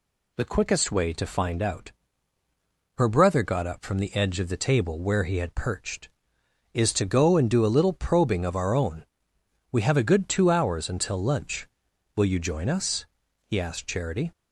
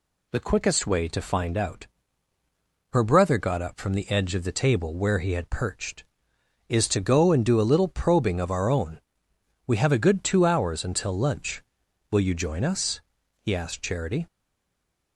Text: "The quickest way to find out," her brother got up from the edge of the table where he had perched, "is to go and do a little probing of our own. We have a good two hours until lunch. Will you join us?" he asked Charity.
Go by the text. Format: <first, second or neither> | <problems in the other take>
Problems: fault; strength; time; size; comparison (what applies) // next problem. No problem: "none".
first | stays silent after the last word; slight; from 14.2 s on; 0.9 s long